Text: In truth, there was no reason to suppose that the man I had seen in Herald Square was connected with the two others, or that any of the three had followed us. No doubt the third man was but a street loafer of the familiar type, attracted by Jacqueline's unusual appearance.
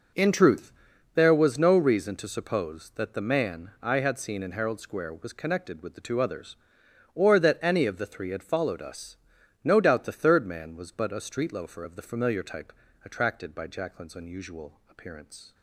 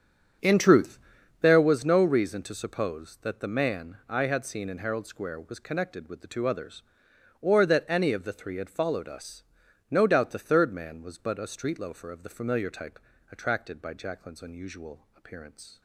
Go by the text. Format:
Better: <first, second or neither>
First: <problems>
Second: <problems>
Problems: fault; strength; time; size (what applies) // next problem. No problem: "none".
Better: first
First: none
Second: starts louder than the rest; until 1.7 s; 7 dB